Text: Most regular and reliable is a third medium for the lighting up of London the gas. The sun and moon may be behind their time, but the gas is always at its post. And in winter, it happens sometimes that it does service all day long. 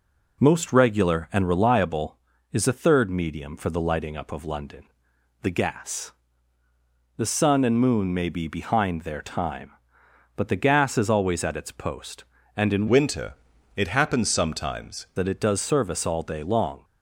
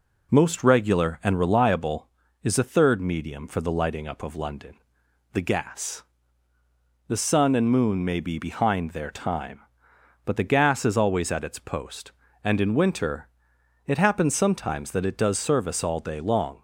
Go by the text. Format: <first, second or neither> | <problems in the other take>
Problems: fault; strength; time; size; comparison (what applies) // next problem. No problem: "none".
second | pauses between "London" and "the"; noticeable; at 4.8 s; 0.58 s long; noticeable in the second // changes voice from "winter" to "sometimes"; from 12.8 to 15.0 s; 2.2 s long